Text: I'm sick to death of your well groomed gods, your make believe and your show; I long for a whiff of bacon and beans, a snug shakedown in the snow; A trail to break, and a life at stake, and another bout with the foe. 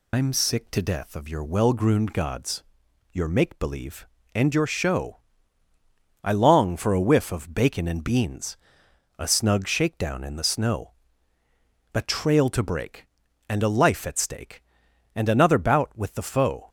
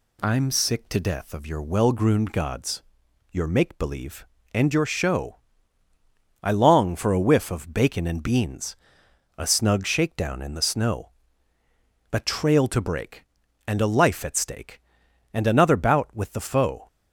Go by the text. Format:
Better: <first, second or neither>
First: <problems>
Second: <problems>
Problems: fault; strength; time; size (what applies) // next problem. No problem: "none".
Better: second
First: loses the start of "I'm"; at 0.1 s; 125 ms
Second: none